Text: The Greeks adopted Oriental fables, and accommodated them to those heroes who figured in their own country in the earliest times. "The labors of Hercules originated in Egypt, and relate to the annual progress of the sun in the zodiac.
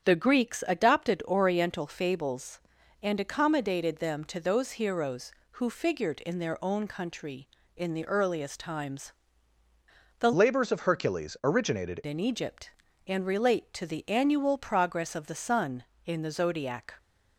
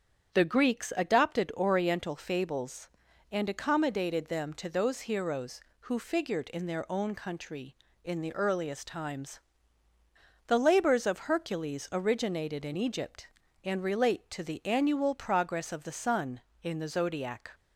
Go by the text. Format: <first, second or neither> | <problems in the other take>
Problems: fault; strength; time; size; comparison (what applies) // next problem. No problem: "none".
second | starts louder than the rest; strong; until 1.0 s; 8.5 dB; strong in the second // changes voice from "labors" to "originated"; from 10.3 to 12.0 s; 1.7 s long